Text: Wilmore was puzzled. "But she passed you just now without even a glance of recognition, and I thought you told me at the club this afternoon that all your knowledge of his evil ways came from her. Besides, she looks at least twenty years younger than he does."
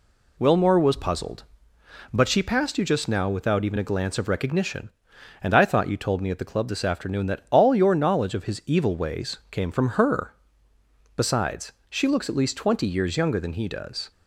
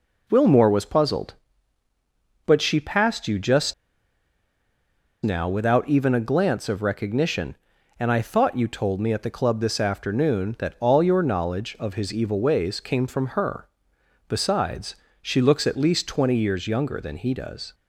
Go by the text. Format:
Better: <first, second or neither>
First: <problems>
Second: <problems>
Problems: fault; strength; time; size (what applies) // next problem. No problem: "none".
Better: first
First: none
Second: pauses between "just" and "now"; strong; at 3.7 s; 1.5 s long